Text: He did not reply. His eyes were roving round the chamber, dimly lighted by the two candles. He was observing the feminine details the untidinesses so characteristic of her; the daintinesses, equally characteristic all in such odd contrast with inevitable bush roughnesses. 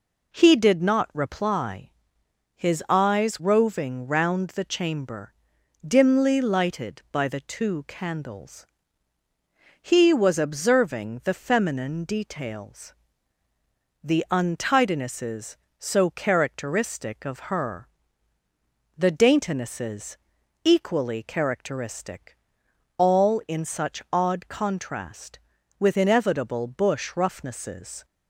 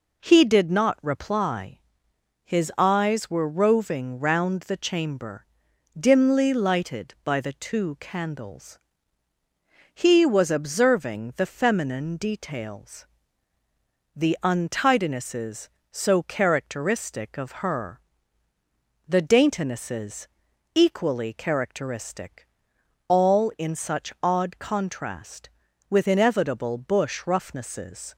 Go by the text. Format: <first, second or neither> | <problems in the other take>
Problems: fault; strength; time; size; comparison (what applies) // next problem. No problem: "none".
second | skips "were"; at 3.3 s // pauses between "details" and "the"; at 12.9 s; 1.0 s long; also in the second // pauses between "characteristic" and "all"; noticeable; at 22.3 s; 0.62 s long; noticeable in the second